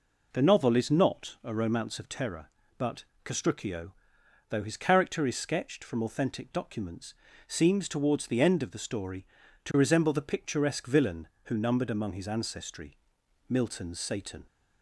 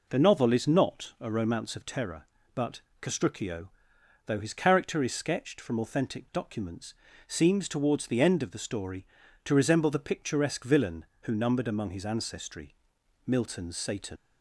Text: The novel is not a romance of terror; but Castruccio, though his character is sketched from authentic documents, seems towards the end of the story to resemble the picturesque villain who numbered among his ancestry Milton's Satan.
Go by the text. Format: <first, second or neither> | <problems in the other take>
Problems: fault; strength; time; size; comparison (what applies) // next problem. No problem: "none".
first | pauses between "but" and "Castruccio"; slight; at 2.7 s; 0.22 s long; slight in the first // pauses between "ancestry" and "Milton's"; noticeable; at 12.7 s; 0.50 s long; noticeable in the first // leaves "Satan" unfinished; at 14.1 s; 70 ms